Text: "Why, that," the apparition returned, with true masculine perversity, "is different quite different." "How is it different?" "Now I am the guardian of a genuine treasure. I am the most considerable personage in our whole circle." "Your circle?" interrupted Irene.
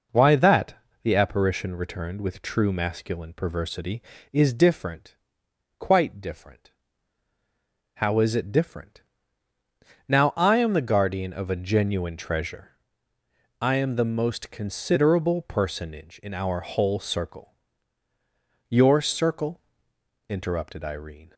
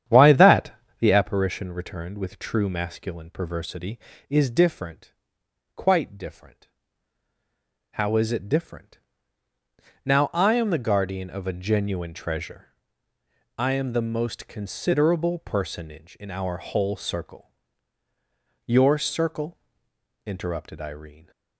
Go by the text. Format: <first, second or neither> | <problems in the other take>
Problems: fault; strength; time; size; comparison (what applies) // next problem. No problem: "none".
first | starts louder than the rest; strong; until 1.3 s; 9.5 dB // pauses between "different" and "quite"; noticeable; at 5.1 s; 0.62 s long; noticeable in the first